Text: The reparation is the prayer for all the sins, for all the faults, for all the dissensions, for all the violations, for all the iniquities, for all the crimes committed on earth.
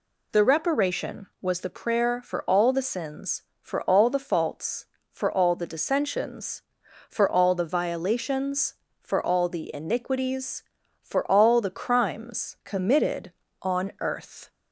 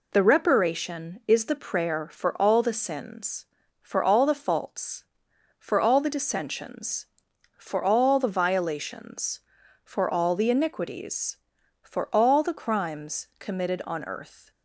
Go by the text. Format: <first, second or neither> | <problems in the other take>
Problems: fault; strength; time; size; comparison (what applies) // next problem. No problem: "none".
second | says "was" for "is"; at 1.4 s